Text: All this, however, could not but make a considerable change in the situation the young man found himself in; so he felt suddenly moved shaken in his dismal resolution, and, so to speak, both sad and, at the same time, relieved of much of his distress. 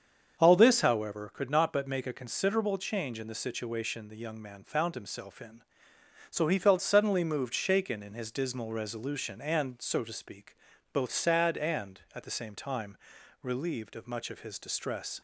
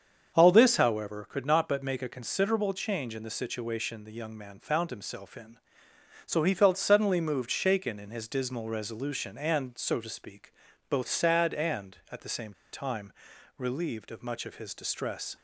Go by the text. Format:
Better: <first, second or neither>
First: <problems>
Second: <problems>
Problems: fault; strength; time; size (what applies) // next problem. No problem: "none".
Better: first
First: starts louder than the rest; strong; until 1.4 s; 7 dB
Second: starts louder than the rest; strong; until 1.3 s; 7 dB // pauses between "same" and "time"; slight; at 12.5 s; 0.19 s long